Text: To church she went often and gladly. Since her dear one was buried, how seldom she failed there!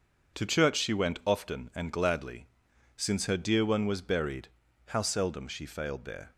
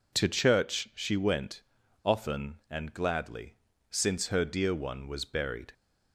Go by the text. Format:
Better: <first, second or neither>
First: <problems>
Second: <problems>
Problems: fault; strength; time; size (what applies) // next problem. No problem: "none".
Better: first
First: none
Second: pauses between "went" and "often"; at 1.6 s; 0.41 s long // stops before "how seldom she failed there"; at 5.7 s